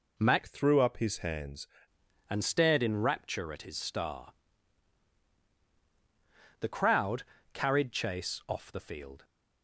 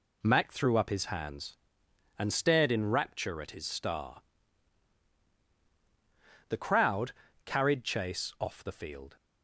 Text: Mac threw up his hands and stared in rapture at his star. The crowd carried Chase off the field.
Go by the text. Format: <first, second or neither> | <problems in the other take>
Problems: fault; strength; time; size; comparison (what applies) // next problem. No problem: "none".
second | changes voice from "threw" to "hands"; from 0.4 to 1.6 s; 1.2 s long // pauses between "crowd" and "carried"; slight; at 7.2 s; 0.30 s long; slight in the second